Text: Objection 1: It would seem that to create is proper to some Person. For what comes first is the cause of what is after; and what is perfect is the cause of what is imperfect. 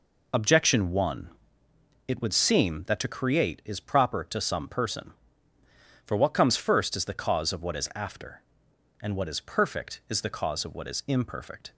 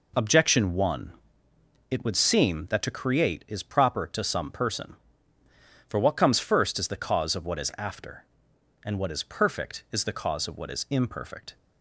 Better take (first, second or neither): second